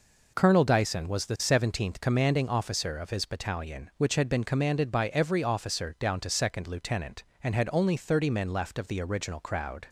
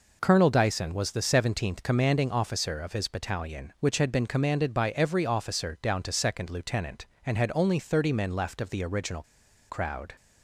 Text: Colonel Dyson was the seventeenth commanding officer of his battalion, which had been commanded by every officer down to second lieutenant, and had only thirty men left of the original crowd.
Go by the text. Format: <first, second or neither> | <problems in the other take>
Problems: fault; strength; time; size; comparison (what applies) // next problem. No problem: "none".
first | pauses between "original" and "crowd"; noticeable; at 9.2 s; 0.47 s long